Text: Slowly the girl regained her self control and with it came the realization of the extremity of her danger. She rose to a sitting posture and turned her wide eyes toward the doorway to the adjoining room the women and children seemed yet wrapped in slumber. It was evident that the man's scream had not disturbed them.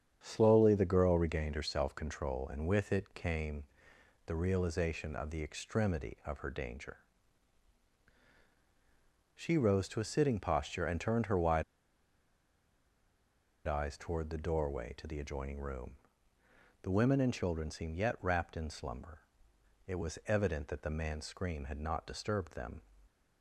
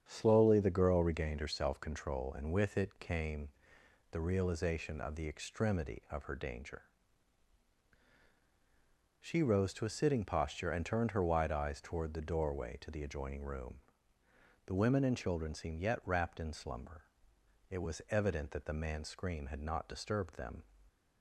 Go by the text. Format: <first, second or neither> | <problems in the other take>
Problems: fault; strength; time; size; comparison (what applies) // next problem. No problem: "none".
second | starts louder than the rest; strong; until 1.2 s; 8 dB; strong in the second // pauses between "came" and "the"; noticeable; at 3.6 s; 0.62 s long; noticeable in the second // pauses between "wide" and "eyes"; strong; at 11.6 s; 2.0 s long // pauses between "room" and "the"; noticeable; at 15.9 s; 0.88 s long; noticeable in the second